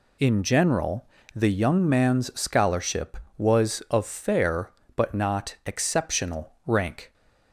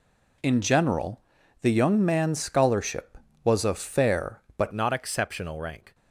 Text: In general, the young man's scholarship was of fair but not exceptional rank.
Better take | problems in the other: first | changes voice at "not"; from 4.7 s on; 1.2 s long

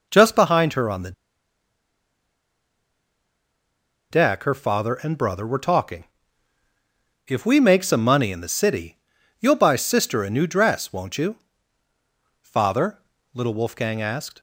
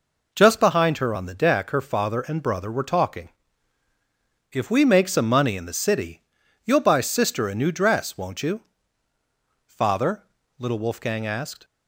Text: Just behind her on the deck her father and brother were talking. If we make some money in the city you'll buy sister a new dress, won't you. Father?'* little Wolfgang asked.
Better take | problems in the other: second | pauses between "the" and "deck"; strong; at 1.1 s; 2.9 s long // pauses between "city" and "you'll"; at 8.9 s; 0.42 s long; also in the second

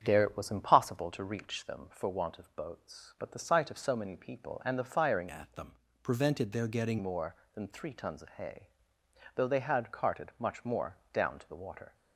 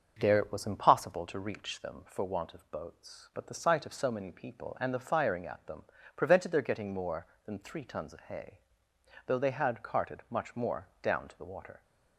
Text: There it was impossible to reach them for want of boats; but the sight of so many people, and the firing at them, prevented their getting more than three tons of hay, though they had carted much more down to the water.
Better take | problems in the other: second | starts louder than the rest; strong; until 1.0 s; 8 dB; also in the second // changes voice from "at" to "getting"; from 5.2 to 6.9 s; 1.7 s long // pauses between "more" and "down"; slight; at 10.9 s; 0.16 s long

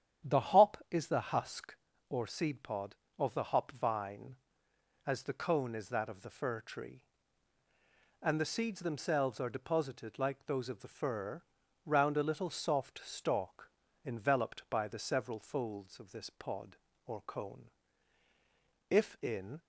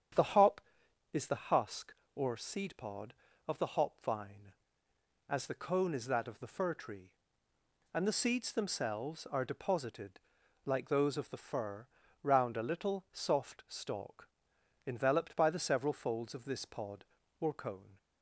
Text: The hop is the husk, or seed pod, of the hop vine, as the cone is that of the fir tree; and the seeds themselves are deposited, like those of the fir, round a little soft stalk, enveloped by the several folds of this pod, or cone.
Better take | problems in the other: second | starts louder than the rest; strong; until 1.3 s; 9.5 dB; strong in the second // goes on to say "If in"; noticeable; from 18.8 s on; 0.70 s long

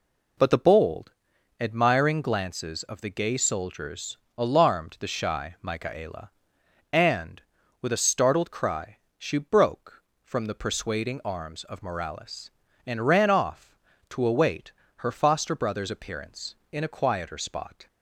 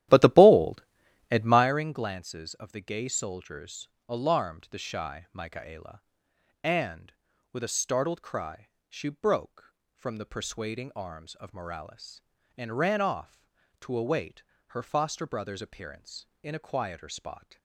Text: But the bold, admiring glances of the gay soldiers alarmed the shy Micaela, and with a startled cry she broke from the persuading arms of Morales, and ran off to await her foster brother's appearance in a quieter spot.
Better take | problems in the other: first | starts louder than the rest; strong; until 1.7 s; 13.5 dB // pauses between "soldiers" and "alarmed"; slight; at 3.8 s; 0.22 s long; slight in the first // pauses between "cry" and "she"; slight; at 8.6 s; 0.22 s long; slight in the first // pauses between "await" and "her"; slight; at 14.4 s; 0.26 s long; slight in the first

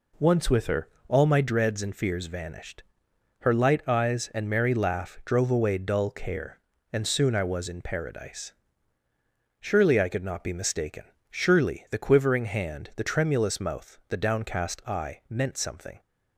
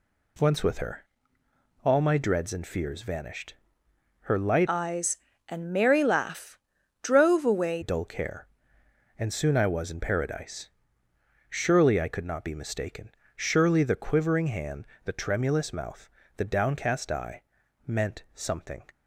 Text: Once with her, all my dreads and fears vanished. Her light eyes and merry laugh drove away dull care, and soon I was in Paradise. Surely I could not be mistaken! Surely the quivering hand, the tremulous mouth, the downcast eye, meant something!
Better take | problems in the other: first | changes voice from "eyes" to "away"; from 4.6 to 7.8 s; 3.2 s long // pauses between "laugh" and "drove"; noticeable; at 6.5 s; 0.46 s long

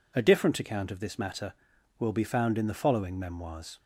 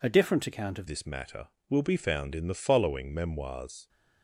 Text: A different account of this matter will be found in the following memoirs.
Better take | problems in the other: first | changes voice at "this"; from 0.8 s on; 3.0 s long

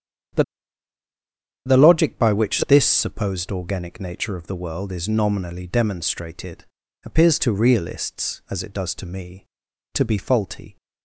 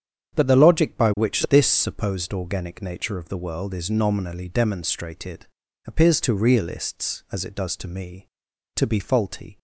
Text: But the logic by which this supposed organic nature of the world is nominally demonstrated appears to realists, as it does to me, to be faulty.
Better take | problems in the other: second | starts louder than the rest; strong; until 2.5 s; 8 dB; strong in the second // pauses between "But" and "the"; at 0.4 s; 1.2 s long // pauses between "demonstrated" and "appears"; at 6.6 s; 0.40 s long; also in the second

